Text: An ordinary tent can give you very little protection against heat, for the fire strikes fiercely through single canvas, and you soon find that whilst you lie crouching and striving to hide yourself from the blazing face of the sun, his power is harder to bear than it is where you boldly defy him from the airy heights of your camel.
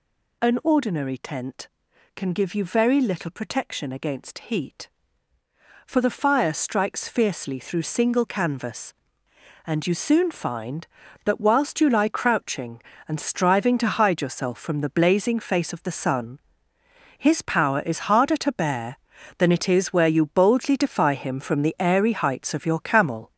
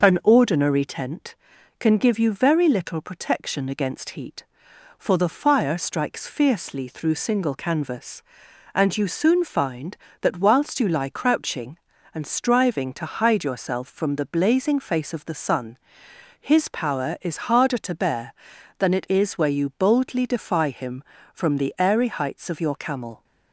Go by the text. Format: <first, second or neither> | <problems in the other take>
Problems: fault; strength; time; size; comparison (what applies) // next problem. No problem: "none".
second | gets louder; noticeable; throughout; 5.5 dB